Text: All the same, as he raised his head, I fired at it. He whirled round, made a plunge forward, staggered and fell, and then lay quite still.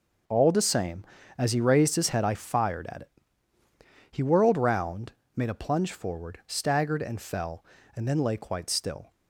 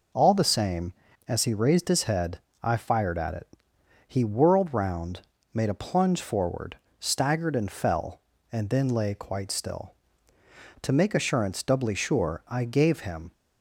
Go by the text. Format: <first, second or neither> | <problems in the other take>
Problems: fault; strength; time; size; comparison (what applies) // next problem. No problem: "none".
first | goes on to say "To make assurance doubly sure I gave him"; strong; from 10.8 s on; 2.5 s long